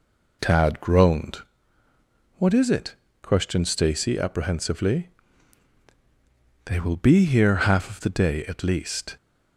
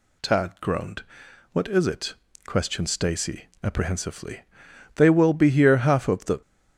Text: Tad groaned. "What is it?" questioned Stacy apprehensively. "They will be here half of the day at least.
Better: first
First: none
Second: pauses between "Stacy" and "apprehensively"; slight; at 3.4 s; 0.18 s long // stops before "day at least"; at 6.4 s

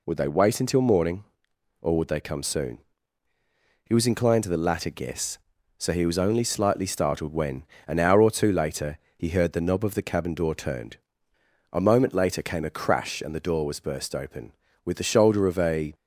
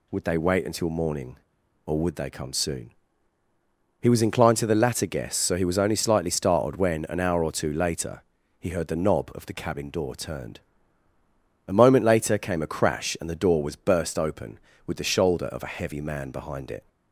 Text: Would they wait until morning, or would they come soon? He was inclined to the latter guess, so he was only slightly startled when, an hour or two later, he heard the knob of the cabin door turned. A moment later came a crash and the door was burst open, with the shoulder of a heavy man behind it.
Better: second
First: stops before "heavy man behind it"; at 15.9 s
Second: none

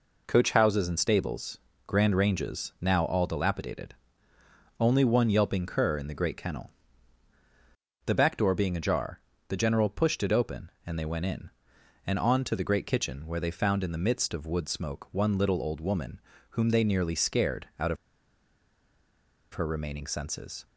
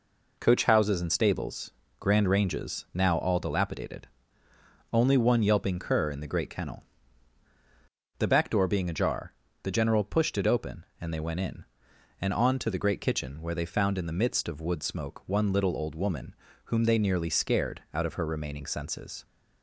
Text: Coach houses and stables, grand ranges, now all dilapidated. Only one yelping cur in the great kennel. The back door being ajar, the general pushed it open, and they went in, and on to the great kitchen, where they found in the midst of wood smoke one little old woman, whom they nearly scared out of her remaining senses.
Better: second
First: pauses between "of" and "her"; strong; at 17.9 s; 1.5 s long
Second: none

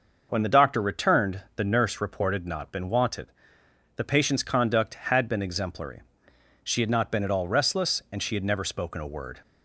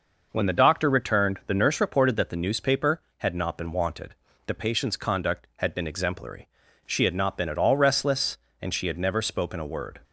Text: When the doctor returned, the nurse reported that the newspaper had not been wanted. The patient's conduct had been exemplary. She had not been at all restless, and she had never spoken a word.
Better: second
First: skips "that the newspaper had"; at 2.4 s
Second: none

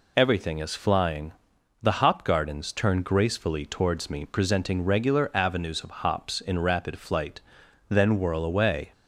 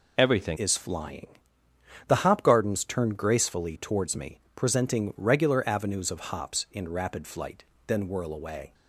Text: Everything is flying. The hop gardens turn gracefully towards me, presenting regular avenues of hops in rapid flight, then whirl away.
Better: first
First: none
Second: changes voice at "is"; from 0.5 s on; 8.2 s long

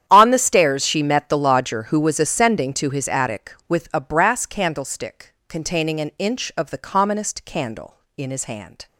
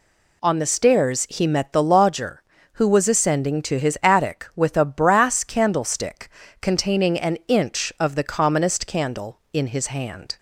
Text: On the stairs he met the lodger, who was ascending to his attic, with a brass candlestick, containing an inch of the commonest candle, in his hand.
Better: second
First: starts louder than the rest; strong; until 1.0 s; 10 dB // says "she" for "he"; at 0.8 s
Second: none

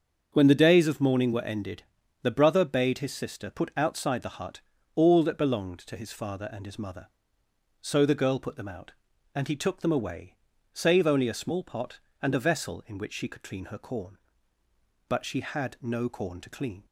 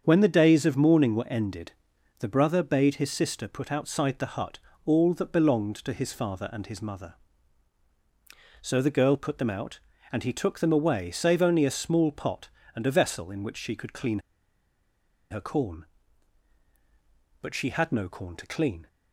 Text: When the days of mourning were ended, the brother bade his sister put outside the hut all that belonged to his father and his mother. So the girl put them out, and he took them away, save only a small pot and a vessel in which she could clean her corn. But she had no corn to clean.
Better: first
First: starts louder than the rest; until 1.3 s; 7 dB // pauses between "hut" and "all"; slight; at 4.6 s; 0.34 s long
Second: starts louder than the rest; strong; until 1.0 s; 7.5 dB // pauses between "hut" and "all"; slight; at 4.5 s; 0.26 s long // pauses between "clean" and "her"; at 14.1 s; 1.1 s long

